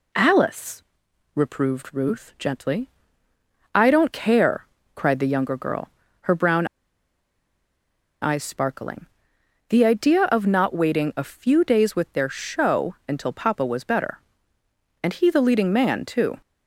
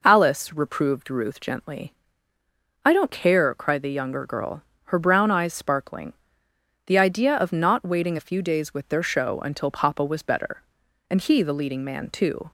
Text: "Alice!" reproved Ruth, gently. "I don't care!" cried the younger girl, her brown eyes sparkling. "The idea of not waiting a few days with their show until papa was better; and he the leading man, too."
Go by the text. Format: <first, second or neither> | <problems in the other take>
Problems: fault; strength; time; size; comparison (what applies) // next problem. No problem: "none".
second | pauses between "brown" and "eyes"; strong; at 6.6 s; 1.5 s long